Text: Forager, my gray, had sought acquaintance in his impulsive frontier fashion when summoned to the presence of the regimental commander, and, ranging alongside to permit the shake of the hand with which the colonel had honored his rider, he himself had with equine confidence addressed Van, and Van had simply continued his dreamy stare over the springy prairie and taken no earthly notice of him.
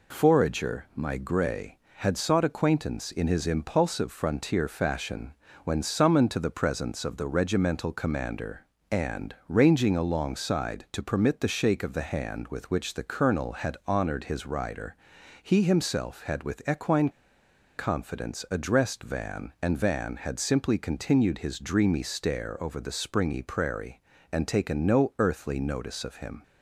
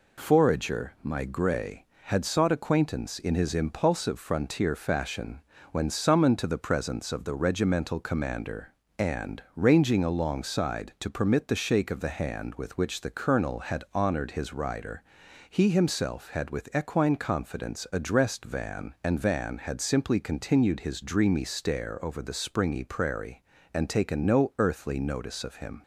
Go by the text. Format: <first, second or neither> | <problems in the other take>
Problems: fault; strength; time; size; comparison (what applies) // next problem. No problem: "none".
second | pauses between "fashion" and "when"; slight; at 5.3 s; 0.30 s long; slight in the second // pauses between "equine" and "confidence"; noticeable; at 17.0 s; 0.67 s long